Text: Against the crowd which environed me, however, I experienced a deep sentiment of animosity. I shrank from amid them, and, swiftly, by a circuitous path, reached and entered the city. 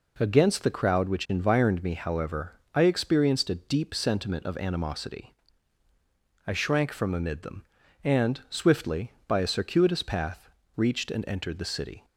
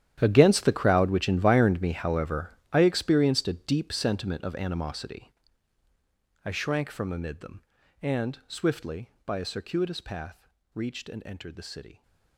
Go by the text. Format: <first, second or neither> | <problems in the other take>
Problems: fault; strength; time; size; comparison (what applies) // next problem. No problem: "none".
first | gets quieter; strong; throughout; 17.5 dB